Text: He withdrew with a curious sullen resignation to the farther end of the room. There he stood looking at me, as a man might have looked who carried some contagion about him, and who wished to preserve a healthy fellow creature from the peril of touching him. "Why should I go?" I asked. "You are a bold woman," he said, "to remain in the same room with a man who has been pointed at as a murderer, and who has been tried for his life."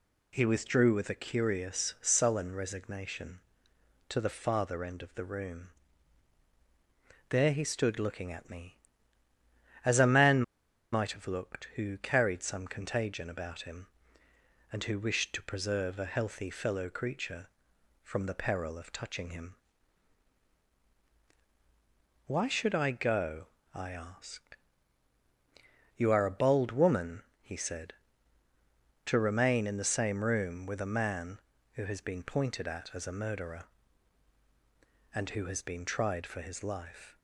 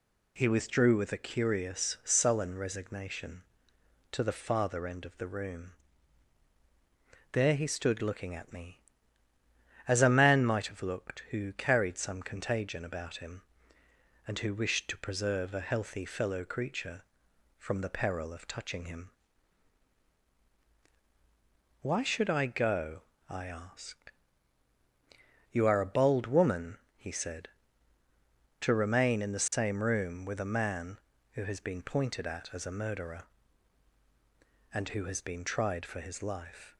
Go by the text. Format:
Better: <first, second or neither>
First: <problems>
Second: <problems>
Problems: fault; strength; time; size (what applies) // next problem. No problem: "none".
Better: second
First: pauses between "man" and "might"; noticeable; at 10.4 s; 0.50 s long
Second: none